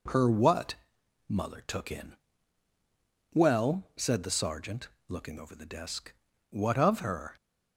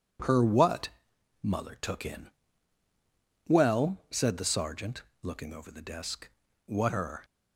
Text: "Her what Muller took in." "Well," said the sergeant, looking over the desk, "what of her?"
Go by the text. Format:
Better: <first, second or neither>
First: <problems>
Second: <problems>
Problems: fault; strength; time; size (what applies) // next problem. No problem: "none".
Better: first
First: pauses between "what" and "Muller"; noticeable; at 0.7 s; 0.52 s long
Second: pauses between "what" and "Muller"; noticeable; at 0.8 s; 0.52 s long // skips "of"; at 6.8 s